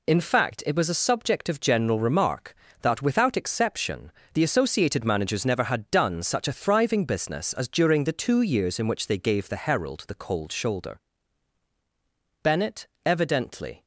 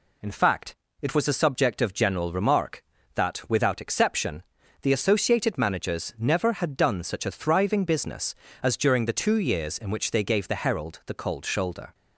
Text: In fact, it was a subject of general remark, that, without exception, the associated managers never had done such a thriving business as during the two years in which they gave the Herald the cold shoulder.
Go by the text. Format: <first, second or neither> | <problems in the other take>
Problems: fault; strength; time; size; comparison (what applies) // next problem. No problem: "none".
second | goes on to say "Bennett evidently"; from 12.4 s on; 1.4 s long